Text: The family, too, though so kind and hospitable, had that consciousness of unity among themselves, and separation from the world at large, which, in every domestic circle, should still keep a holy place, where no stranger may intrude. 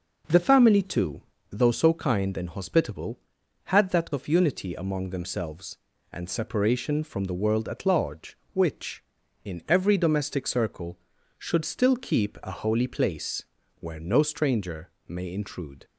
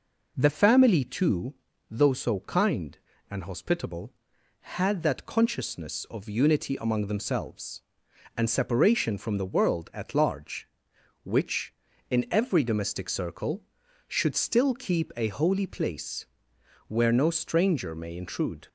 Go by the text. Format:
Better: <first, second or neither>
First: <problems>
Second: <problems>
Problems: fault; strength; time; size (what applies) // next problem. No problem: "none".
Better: second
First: skips "consciousness"; at 4.1 s // pauses between "stranger" and "may"; slight; at 14.8 s; 0.18 s long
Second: none